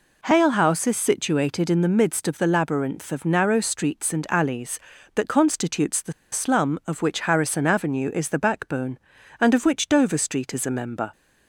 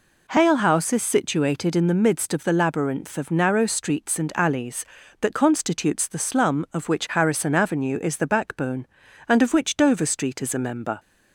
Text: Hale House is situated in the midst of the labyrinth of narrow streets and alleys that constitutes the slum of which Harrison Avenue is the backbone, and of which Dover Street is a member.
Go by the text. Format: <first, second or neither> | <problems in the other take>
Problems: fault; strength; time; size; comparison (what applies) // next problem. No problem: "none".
second | pauses between "the" and "slum"; slight; at 6.1 s; 0.19 s long